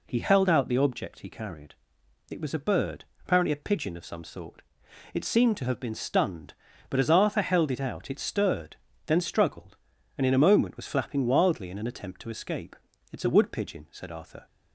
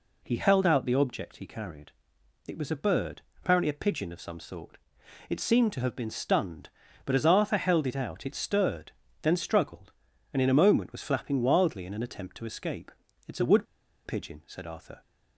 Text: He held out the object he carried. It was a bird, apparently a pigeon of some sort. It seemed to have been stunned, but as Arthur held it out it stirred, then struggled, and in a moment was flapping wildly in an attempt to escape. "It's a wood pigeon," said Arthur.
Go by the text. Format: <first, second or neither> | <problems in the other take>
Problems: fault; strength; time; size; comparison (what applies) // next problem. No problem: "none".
first | pauses between "wood" and "pigeon"; at 13.6 s; 0.40 s long